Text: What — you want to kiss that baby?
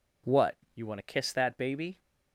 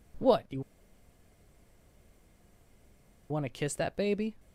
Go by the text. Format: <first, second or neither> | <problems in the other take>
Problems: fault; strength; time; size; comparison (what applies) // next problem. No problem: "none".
first | pauses between "you" and "want"; strong; at 0.6 s; 2.6 s long